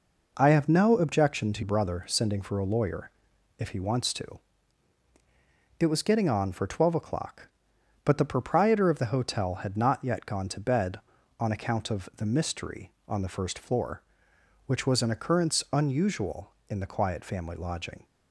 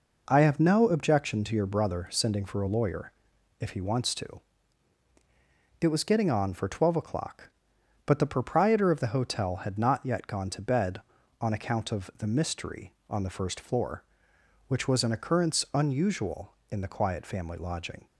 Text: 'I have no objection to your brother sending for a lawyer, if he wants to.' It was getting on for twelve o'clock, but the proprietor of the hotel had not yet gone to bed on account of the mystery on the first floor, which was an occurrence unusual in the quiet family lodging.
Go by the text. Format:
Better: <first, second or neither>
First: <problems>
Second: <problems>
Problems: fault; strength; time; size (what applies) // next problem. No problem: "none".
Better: second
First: skips "your"; at 1.6 s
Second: none